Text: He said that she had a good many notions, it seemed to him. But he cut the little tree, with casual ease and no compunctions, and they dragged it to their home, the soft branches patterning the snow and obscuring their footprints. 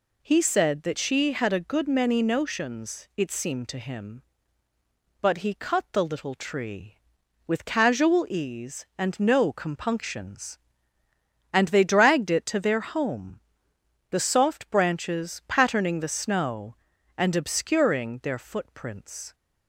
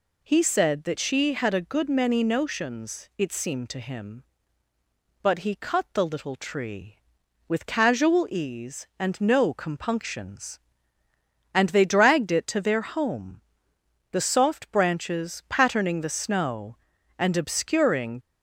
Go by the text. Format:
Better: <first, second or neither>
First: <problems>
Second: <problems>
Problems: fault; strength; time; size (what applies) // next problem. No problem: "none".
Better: first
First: none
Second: stops before "their footprints"; at 18.2 s